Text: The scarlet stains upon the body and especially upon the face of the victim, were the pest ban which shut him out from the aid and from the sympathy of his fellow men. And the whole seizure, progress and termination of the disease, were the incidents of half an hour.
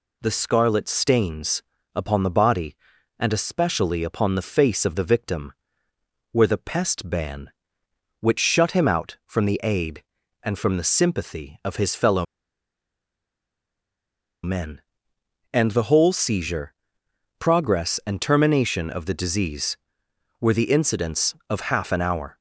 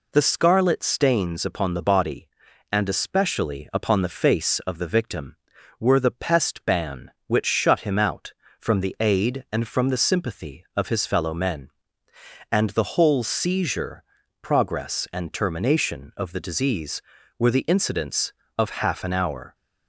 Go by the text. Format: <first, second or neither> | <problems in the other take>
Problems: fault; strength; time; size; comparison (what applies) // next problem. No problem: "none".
second | pauses between "stains" and "upon"; slight; at 1.6 s; 0.34 s long // pauses between "fellow" and "men"; strong; at 12.2 s; 2.1 s long